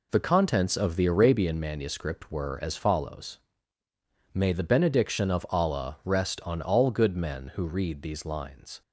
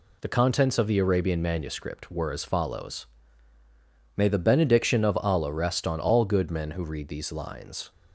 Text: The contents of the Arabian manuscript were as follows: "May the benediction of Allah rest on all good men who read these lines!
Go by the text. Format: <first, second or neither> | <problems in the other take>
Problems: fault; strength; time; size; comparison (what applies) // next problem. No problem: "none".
second | gets quieter; strong; throughout; 7.5 dB